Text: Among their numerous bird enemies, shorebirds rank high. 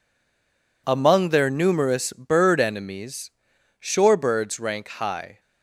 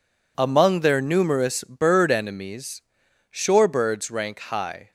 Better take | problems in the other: second | stays silent before the first word; slight; until 0.8 s; 0.8 s long

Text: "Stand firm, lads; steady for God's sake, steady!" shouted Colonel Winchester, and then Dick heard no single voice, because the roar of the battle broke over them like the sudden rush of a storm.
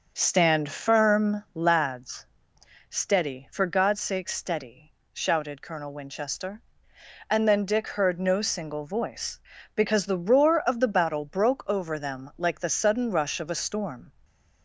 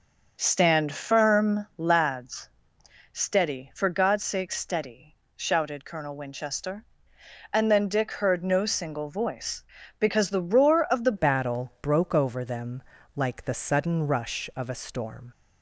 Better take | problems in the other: first | starts louder than the rest; until 1.3 s; 6.5 dB; also in the first // changes voice at "battle"; from 11.1 s on; 4.2 s long // pauses between "them" and "like"; slight; at 12.8 s; 0.32 s long

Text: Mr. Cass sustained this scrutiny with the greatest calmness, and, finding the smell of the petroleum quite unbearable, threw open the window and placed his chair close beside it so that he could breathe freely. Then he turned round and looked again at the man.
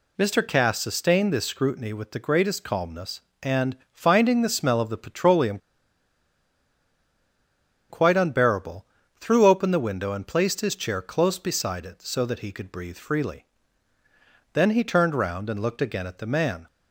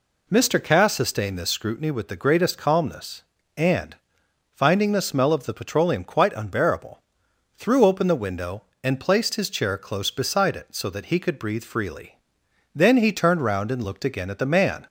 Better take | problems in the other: second | pauses between "petroleum" and "quite"; strong; at 5.5 s; 2.3 s long

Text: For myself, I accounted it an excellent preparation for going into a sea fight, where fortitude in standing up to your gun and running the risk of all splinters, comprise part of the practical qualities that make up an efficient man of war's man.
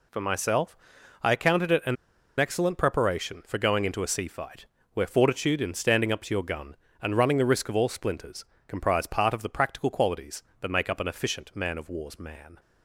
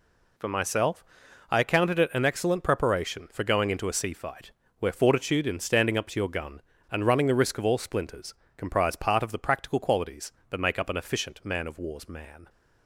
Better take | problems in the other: second | pauses between "an" and "excellent"; at 1.9 s; 0.44 s long

